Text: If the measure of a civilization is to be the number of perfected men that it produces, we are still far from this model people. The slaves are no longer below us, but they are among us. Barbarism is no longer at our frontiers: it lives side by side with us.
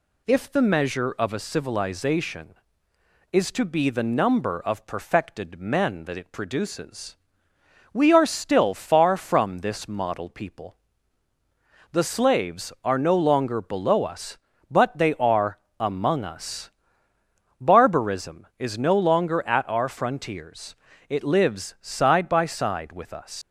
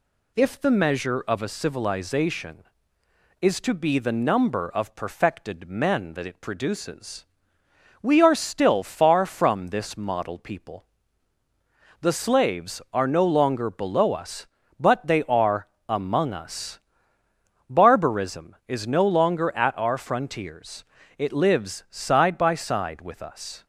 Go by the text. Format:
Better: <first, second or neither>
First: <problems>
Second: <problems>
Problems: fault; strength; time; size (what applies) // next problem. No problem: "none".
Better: second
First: pauses between "are" and "among"; slight; at 15.5 s; 0.22 s long // leaves "us" unfinished; at 23.4 s; 145 ms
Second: pauses between "are" and "among"; slight; at 15.6 s; 0.22 s long